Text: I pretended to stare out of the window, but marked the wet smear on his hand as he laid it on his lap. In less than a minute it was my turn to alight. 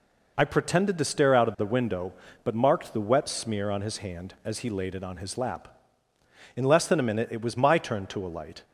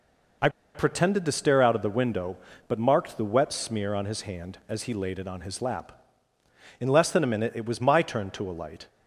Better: first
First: none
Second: pauses between "I" and "pretended"; slight; at 0.4 s; 0.26 s long

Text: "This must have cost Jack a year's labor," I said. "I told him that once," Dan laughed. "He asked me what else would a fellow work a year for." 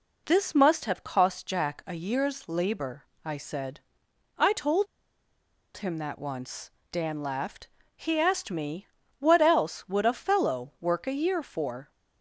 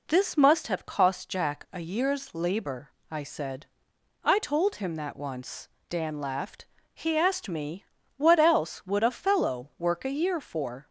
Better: second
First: pauses between "told" and "him"; noticeable; at 4.8 s; 0.90 s long // pauses between "me" and "what"; slight; at 8.8 s; 0.32 s long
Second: pauses between "me" and "what"; slight; at 7.8 s; 0.32 s long

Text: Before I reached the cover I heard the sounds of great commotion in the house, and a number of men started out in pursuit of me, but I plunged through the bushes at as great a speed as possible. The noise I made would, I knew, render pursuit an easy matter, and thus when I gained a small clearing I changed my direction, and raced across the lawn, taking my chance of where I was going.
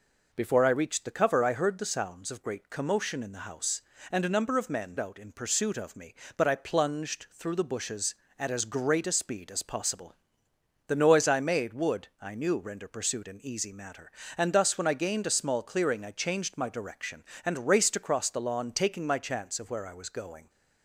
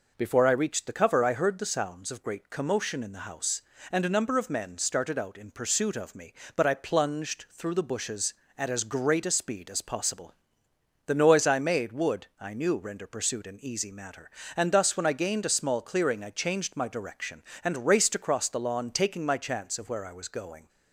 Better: second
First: skips "started"; at 4.9 s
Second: none

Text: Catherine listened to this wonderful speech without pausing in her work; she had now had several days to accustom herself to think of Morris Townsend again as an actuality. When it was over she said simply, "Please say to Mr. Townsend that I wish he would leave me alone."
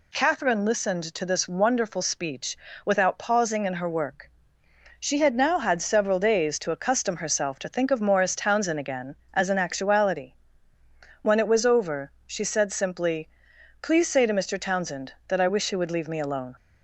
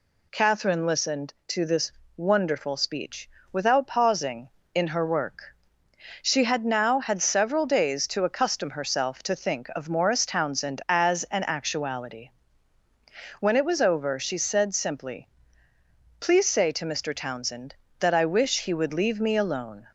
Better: first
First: pauses between "speech" and "without"; slight; at 2.5 s; 0.26 s long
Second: pauses between "this" and "wonderful"; slight; at 1.9 s; 0.24 s long // pauses between "speech" and "without"; slight; at 3.2 s; 0.24 s long // skips "again"; at 10.8 s

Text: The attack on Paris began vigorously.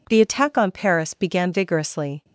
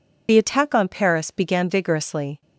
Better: first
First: none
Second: loses the start of "The"; at 0.2 s; 50 ms

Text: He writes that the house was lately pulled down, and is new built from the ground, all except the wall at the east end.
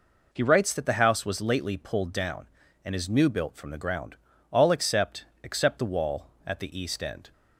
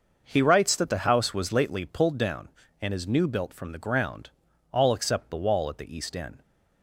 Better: second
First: says "except" twice; at 5.4 s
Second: none

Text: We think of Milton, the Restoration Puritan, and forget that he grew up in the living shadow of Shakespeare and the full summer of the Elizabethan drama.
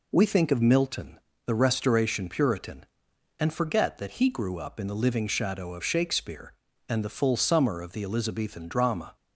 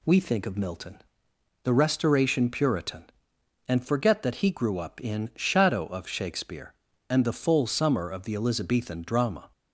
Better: first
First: none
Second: skips "the living"; at 5.3 s

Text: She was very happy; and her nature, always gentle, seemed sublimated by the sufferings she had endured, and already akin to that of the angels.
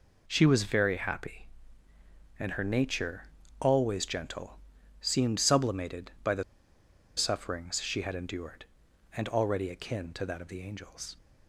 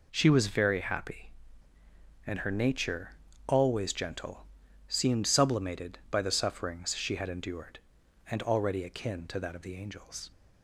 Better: second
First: pauses between "the" and "sufferings"; noticeable; at 6.4 s; 0.75 s long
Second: none

